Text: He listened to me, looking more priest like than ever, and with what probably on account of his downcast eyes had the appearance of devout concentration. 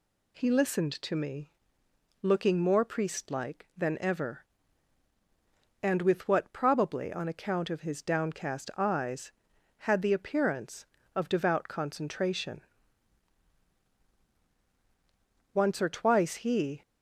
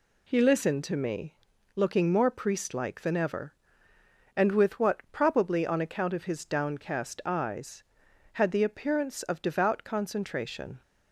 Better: second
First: goes on to say "Once or twice he"; noticeable; from 15.5 s on; 1.2 s long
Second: none

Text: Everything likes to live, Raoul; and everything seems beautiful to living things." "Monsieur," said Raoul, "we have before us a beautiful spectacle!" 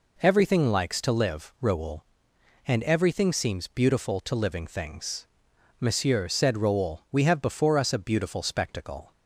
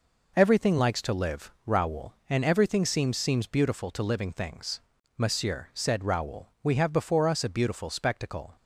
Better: first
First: none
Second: says "seems" twice; at 3.1 s

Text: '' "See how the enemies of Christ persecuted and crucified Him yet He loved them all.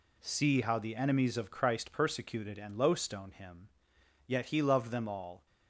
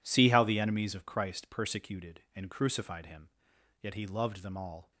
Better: second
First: says "lowstone" for "crucified"; at 2.7 s // pauses between "Him" and "yet"; noticeable; at 3.6 s; 0.58 s long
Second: pauses between "Him" and "yet"; noticeable; at 3.2 s; 0.52 s long

